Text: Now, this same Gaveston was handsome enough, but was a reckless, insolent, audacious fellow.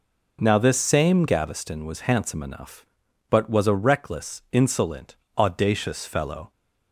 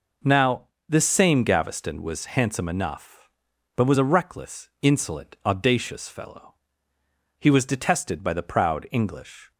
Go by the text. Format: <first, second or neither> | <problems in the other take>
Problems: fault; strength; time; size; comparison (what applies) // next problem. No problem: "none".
first | goes on to say "He was detested by the proud English"; strong; from 7.3 s on; 2.1 s long